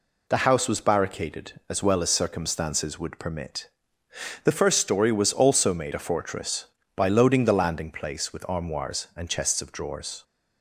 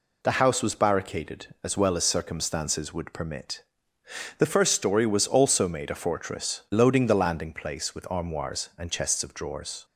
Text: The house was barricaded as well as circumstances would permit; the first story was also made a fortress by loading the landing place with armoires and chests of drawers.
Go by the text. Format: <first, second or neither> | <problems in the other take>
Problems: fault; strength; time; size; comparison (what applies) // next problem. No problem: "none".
first | skips "by"; at 6.6 s